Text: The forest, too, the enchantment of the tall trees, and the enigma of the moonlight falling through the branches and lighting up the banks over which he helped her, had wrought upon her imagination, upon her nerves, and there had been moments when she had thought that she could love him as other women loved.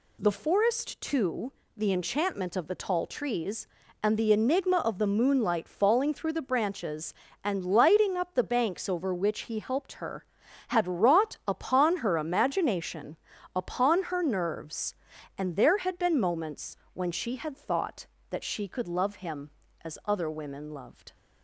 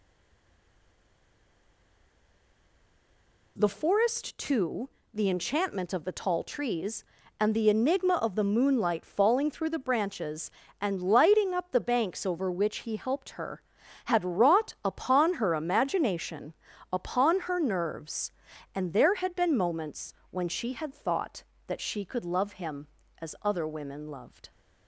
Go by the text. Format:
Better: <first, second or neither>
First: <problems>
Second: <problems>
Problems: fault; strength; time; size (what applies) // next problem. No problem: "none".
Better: first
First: pauses between "moments" and "when"; slight; at 16.7 s; 0.16 s long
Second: stays silent before the first word; strong; until 3.5 s; 3.5 s long // pauses between "moments" and "when"; slight; at 20.1 s; 0.16 s long